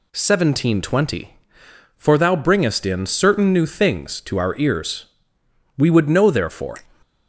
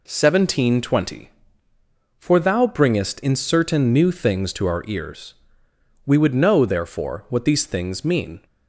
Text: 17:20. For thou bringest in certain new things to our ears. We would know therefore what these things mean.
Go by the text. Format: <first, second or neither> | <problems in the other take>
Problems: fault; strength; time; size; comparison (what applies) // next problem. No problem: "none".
second | stops before "what these things mean"; at 7.0 s